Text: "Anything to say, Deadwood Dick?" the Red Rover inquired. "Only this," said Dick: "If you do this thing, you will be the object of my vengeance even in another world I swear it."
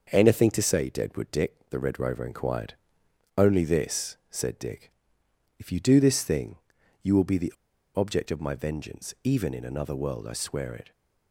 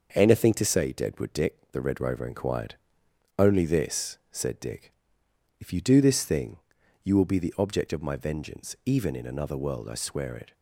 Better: second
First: starts louder than the rest; until 1.1 s; 6 dB // pauses between "the" and "object"; at 7.5 s; 0.43 s long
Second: starts louder than the rest; until 1.1 s; 6 dB

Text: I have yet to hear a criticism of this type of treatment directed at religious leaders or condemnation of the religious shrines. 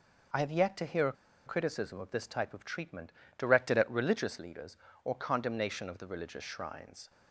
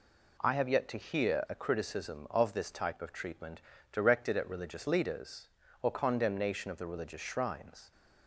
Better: second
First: pauses between "a" and "criticism"; slight; at 1.1 s; 0.33 s long // pauses between "treatment" and "directed"; slight; at 3.1 s; 0.26 s long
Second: pauses between "treatment" and "directed"; slight; at 3.6 s; 0.30 s long

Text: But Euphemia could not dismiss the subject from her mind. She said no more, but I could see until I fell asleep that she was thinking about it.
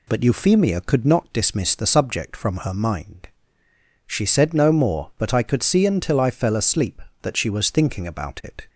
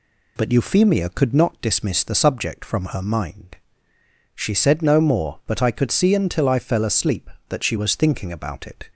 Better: neither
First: none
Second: none

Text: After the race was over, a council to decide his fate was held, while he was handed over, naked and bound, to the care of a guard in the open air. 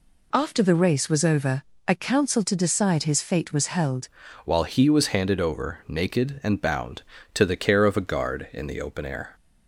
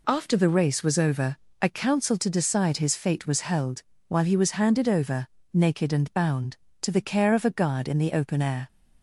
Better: second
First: changes voice at "while"; from 4.4 s on; 4.9 s long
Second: none

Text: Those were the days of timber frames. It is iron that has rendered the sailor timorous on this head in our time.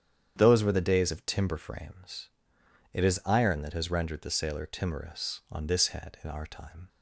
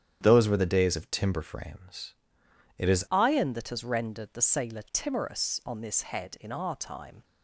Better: first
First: starts louder than the rest; strong; until 1.3 s; 9 dB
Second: starts louder than the rest; strong; until 1.2 s; 9 dB // changes voice at "iron"; from 3.1 s on; 4.1 s long

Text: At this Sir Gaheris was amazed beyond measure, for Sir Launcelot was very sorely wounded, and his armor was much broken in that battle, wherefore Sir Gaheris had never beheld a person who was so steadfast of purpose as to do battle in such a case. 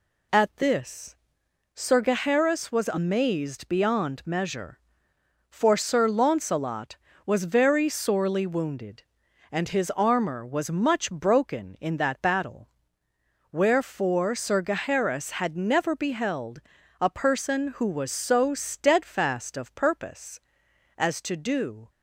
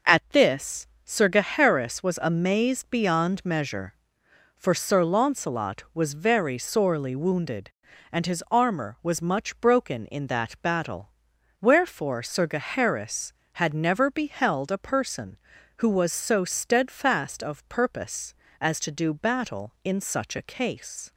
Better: second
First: pauses between "this" and "Sir"; noticeable; at 1.1 s; 0.58 s long // pauses between "beheld" and "a"; at 16.6 s; 0.40 s long // stops before "battle in such a case"; at 21.8 s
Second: pauses between "this" and "Sir"; slight; at 0.8 s; 0.20 s long

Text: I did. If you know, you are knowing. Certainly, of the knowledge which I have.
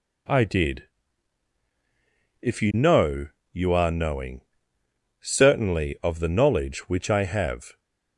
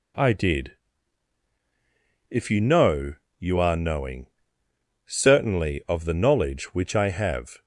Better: neither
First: none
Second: none

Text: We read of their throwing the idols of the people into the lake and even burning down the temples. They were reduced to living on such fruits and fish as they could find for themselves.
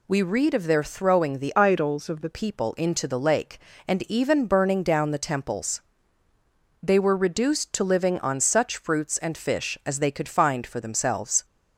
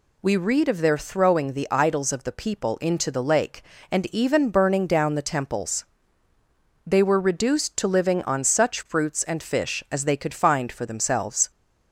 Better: second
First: changes voice from "idols" to "the"; from 1.5 to 2.3 s; 0.8 s long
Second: none

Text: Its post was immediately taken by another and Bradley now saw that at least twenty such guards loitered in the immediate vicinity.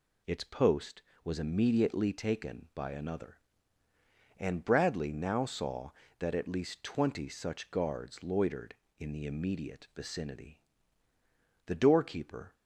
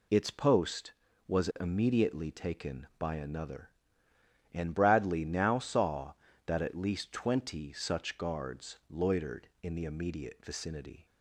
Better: second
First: goes on to say "The doorkeeper"; noticeable; from 11.6 s on; 0.90 s long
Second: none

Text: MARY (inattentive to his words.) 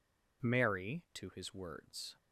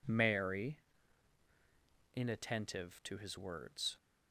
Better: second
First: skips "inattentive"; at 1.0 s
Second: none

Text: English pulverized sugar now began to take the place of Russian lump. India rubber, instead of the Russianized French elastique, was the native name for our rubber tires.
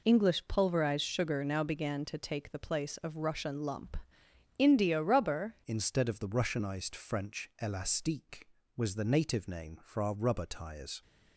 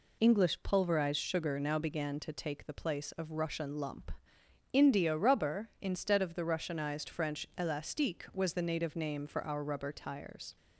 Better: second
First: changes voice at "instead"; from 5.6 s on; 5.4 s long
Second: none

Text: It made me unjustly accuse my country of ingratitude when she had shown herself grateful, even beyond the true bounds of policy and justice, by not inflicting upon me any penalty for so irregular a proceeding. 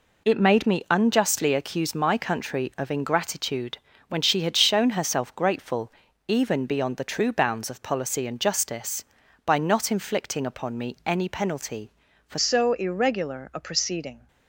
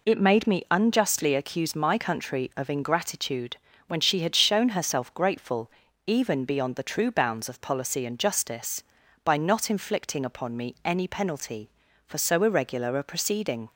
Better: second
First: pauses between "ingratitude" and "when"; slight; at 3.7 s; 0.32 s long // changes voice at "so"; from 12.3 s on; 1.9 s long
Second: pauses between "ingratitude" and "when"; slight; at 3.5 s; 0.32 s long

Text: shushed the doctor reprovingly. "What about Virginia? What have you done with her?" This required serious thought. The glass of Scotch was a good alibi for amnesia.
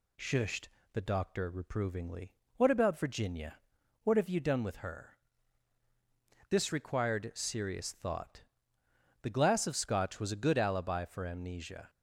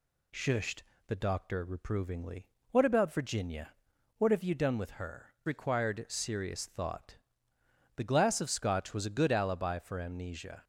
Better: first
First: pauses between "shushed" and "the"; slight; at 0.6 s; 0.26 s long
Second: pauses between "shushed" and "the"; slight; at 0.8 s; 0.26 s long // skips "This"; at 5.3 s

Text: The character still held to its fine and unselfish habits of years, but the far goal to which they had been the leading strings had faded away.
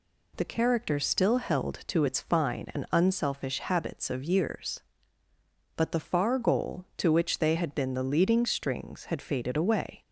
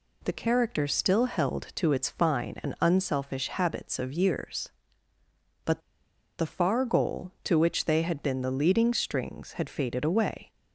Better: first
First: none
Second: pauses between "but" and "the"; noticeable; at 5.8 s; 0.58 s long

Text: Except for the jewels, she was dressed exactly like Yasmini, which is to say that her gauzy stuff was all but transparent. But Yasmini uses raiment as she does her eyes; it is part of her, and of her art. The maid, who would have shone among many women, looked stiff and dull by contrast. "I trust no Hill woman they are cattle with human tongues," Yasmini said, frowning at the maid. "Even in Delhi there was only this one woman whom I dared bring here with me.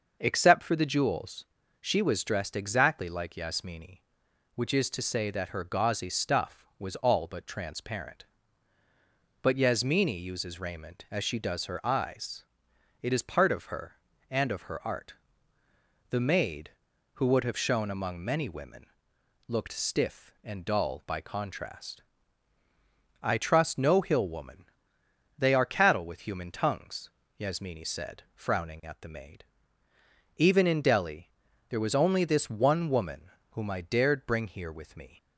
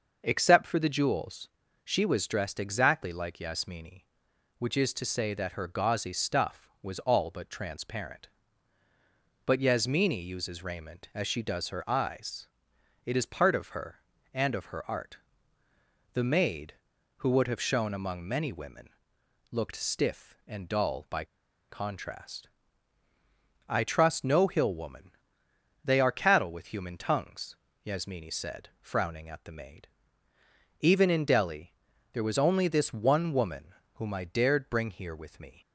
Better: first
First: starts louder than the rest; until 1.2 s; 6 dB // pauses between "woman" and "they"; noticeable; at 24.6 s; 0.76 s long // pauses between "Delhi" and "there"; at 31.3 s; 0.38 s long // pauses between "woman" and "whom"; slight; at 33.3 s; 0.20 s long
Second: starts louder than the rest; until 1.2 s; 6 dB // pauses between "by" and "contrast"; at 21.2 s; 0.45 s long // pauses between "woman" and "they"; noticeable; at 25.1 s; 0.76 s long // pauses between "Delhi" and "there"; at 31.7 s; 0.38 s long // pauses between "woman" and "whom"; slight; at 33.7 s; 0.20 s long

